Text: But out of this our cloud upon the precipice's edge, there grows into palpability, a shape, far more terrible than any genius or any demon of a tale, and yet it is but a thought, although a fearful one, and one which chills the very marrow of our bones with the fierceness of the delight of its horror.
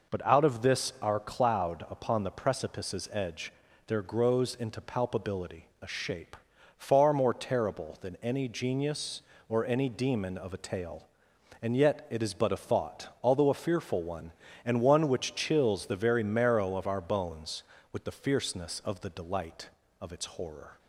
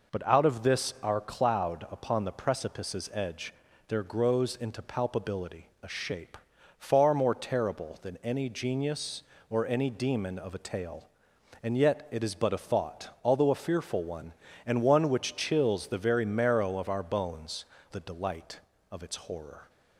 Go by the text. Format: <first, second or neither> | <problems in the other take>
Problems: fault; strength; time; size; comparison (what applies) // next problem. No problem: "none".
first | skips "with the fierceness of"; at 17.7 s